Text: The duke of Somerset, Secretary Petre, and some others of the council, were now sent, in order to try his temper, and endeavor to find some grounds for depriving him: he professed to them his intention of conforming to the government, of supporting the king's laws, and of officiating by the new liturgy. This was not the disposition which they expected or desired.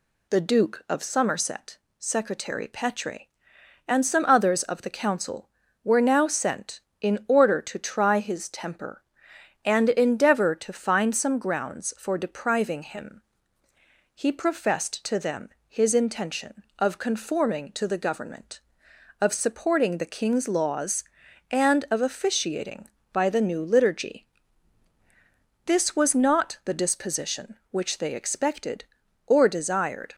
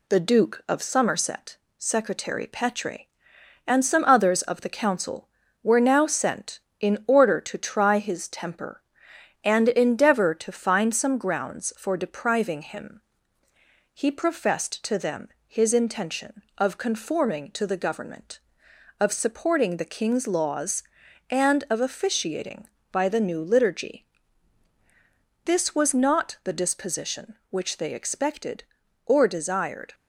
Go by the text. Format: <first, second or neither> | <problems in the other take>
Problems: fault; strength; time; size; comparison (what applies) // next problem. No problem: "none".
first | gets quieter; slight; throughout; 2.5 dB // pauses between "them" and "his"; slight; at 15.2 s; 0.18 s long; slight in the first